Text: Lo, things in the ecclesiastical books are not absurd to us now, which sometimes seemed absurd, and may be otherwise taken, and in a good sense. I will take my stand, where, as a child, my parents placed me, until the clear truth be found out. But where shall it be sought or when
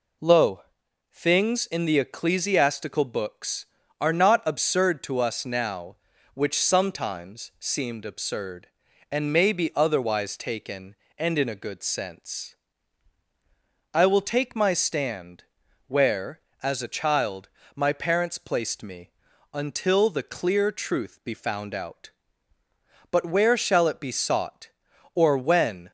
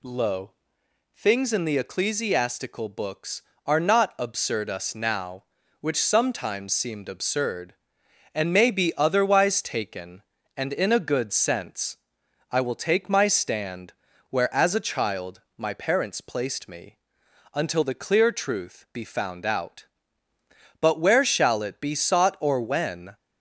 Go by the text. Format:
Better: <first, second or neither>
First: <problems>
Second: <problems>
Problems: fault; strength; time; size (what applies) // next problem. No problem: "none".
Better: first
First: none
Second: skips "to"; at 4.6 s